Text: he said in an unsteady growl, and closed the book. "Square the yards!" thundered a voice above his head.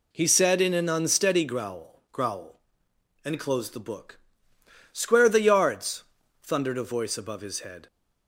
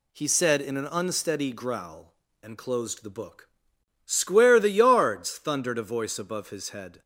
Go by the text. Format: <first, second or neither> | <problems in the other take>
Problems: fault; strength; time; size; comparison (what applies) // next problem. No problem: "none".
second | says "growl" twice; at 2.1 s